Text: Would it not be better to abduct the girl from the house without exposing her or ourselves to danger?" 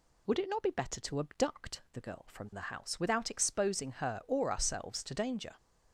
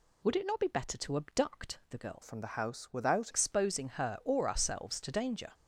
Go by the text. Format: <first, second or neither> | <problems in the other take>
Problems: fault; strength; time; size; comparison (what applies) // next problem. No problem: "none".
first | changes voice from "from" to "without"; from 2.2 to 3.3 s; 1.1 s long